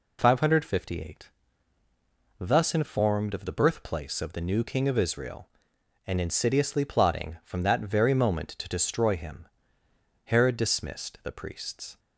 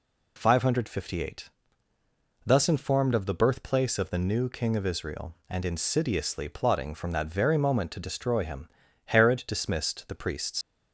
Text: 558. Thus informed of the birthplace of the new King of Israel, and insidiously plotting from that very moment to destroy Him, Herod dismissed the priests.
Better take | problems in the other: first | leaves "priests" unfinished; at 10.6 s; 70 ms

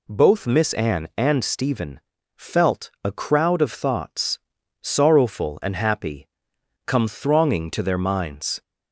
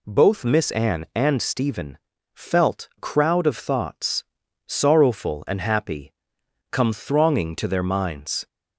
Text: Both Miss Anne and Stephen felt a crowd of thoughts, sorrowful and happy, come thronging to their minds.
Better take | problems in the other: first | pauses between "Stephen" and "felt"; at 1.9 s; 0.38 s long; also in the first // skips "a"; at 2.9 s

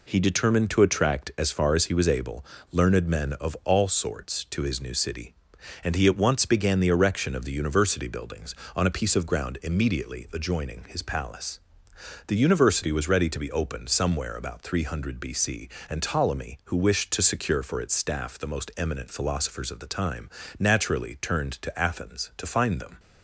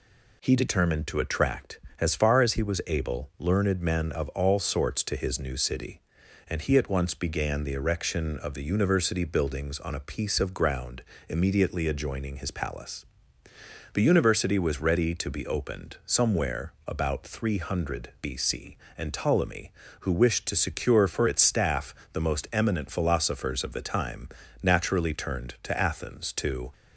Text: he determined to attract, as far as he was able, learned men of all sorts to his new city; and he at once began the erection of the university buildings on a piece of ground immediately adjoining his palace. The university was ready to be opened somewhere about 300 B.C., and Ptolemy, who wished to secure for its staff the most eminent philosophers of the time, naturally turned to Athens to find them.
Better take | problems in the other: first | pauses between "ground" and "immediately"; slight; at 11.0 s; 0.26 s long // pauses between "staff" and "the"; slight; at 21.9 s; 0.20 s long // stops before "find them"; at 26.7 s

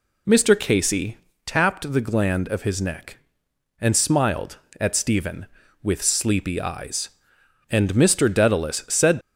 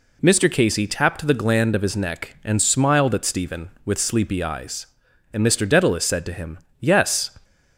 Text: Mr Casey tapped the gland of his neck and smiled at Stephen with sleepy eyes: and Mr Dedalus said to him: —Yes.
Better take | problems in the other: second | pauses between "Casey" and "tapped"; slight; at 1.1 s; 0.28 s long // stops before "to him Yes"; at 9.2 s

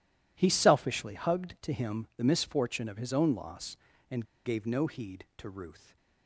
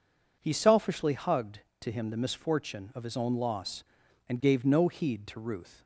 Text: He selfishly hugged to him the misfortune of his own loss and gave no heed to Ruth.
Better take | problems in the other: second | pauses between "and" and "gave"; slight; at 4.2 s; 0.20 s long

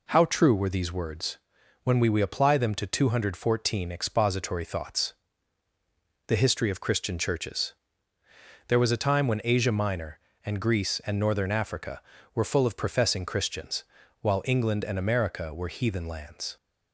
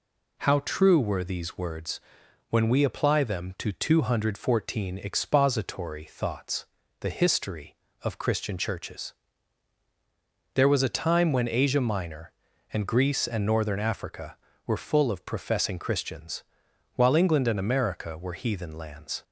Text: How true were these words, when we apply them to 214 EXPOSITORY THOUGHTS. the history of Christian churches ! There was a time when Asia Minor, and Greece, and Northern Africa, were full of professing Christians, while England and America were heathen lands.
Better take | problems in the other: second | says "we" twice; at 2.0 s

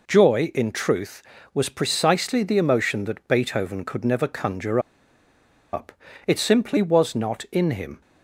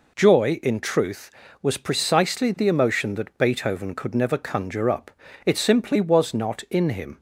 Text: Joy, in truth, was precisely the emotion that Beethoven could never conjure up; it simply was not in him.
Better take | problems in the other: second | pauses between "conjure" and "up"; noticeable; at 4.7 s; 0.93 s long

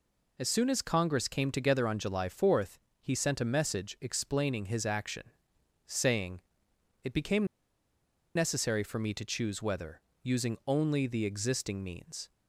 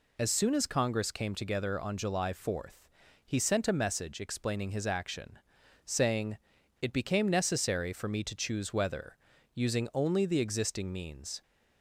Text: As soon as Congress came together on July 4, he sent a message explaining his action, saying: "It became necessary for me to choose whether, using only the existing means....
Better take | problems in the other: second | pauses between "became" and "necessary"; noticeable; at 7.4 s; 0.90 s long

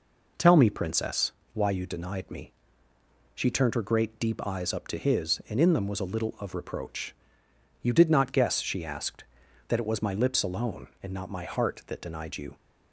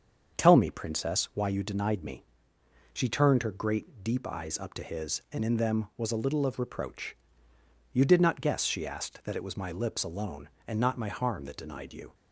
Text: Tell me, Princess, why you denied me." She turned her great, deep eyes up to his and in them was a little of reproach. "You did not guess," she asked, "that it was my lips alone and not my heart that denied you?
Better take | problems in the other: first | starts louder than the rest; until 1.4 s; 7 dB // says "harm" for "heart"; at 11.0 s

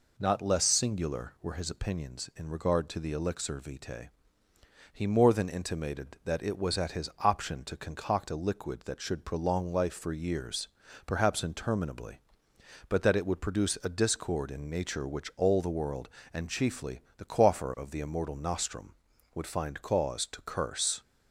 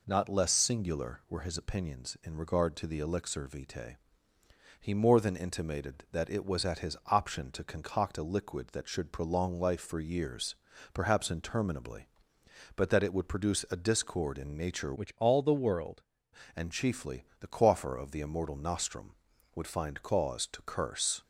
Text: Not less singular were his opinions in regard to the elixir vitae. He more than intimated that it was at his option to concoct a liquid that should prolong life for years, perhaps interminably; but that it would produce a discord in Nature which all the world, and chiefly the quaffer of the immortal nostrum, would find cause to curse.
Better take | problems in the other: first | changes voice from "which" to "world"; from 14.9 to 16.0 s; 1.1 s long // pauses between "chiefly" and "the"; slight; at 17.2 s; 0.16 s long; slight in the first

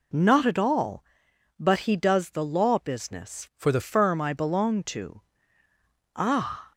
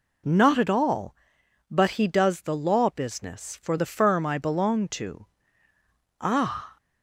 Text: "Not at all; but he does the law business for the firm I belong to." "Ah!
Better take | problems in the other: second | changes voice from "for" to "the"; from 3.5 to 3.7 s; 0.2 s long

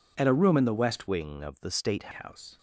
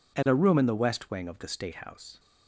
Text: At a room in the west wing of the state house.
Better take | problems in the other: second | changes voice from "wing" to "state"; from 1.0 to 2.1 s; 1.1 s long

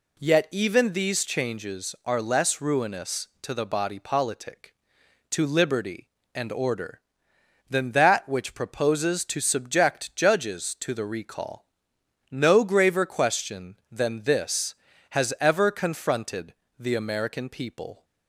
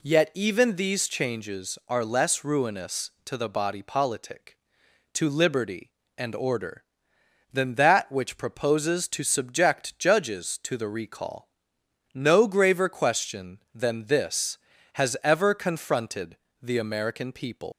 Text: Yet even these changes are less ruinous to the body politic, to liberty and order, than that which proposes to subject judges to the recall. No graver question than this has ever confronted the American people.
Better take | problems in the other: first | pauses between "confronted" and "the"; slight; at 16.3 s; 0.24 s long; slight in the first // leaves "people" unfinished; at 17.7 s; 150 ms

